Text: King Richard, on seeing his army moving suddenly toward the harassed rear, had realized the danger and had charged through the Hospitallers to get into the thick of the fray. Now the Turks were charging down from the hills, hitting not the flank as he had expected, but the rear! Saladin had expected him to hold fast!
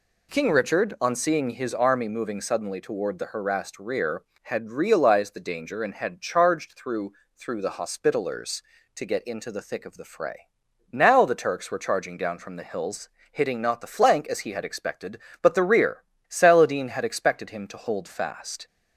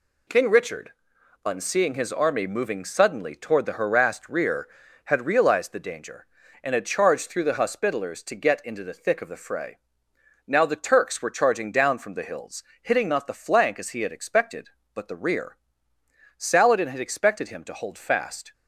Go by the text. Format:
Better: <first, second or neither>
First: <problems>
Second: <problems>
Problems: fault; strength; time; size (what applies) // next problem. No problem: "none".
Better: second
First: says "through" twice; at 7.3 s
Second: none